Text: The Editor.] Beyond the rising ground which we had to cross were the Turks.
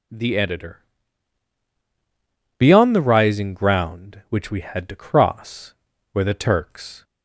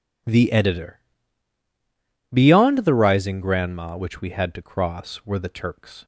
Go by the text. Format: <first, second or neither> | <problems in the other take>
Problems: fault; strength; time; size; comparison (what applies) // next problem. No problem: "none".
first | says "grandma" for "ground"; at 3.4 s